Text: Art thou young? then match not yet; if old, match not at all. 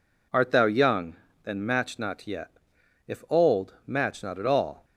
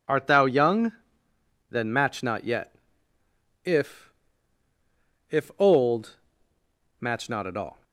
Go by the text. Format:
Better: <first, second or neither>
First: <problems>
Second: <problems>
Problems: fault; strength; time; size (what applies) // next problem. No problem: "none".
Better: first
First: none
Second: says "if" twice; at 5.3 s